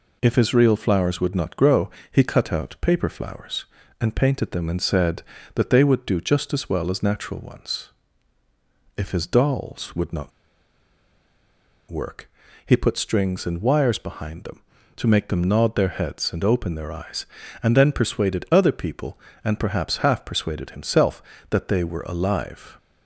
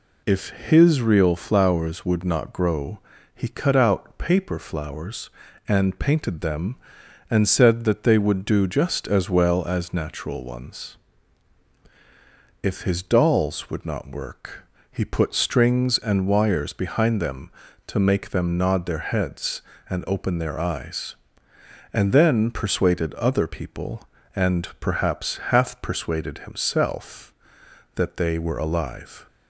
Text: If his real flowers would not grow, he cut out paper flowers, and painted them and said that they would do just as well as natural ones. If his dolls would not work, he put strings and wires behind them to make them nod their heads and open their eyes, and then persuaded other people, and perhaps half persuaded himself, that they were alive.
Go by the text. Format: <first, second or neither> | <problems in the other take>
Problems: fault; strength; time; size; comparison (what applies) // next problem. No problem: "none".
second | pauses between "not" and "work"; strong; at 10.3 s; 1.6 s long